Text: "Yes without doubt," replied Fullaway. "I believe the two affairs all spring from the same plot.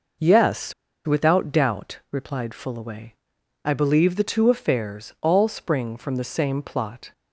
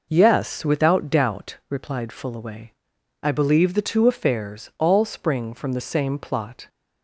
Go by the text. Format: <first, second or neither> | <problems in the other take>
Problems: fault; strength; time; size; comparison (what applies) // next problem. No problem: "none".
second | pauses between "Yes" and "without"; slight; at 0.7 s; 0.32 s long